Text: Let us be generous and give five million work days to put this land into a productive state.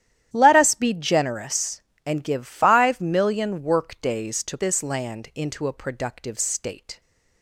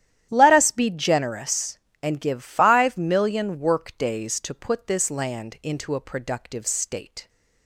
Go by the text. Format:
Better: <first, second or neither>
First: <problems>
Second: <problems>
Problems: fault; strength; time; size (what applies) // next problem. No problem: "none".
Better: second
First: starts louder than the rest; strong; until 1.3 s; 11.5 dB // skips "put"; at 4.5 s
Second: starts louder than the rest; strong; until 1.3 s; 11 dB